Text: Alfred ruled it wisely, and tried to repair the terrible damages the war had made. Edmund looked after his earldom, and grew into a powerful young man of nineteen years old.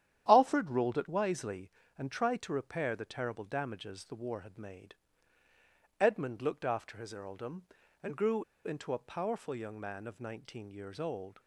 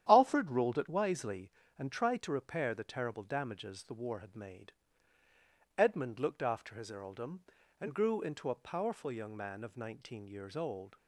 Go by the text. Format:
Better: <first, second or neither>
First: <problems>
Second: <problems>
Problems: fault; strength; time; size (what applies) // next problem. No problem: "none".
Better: second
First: starts louder than the rest; strong; until 1.2 s; 10.5 dB // pauses between "grew" and "into"; slight; at 8.4 s; 0.22 s long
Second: starts louder than the rest; strong; until 1.1 s; 10.5 dB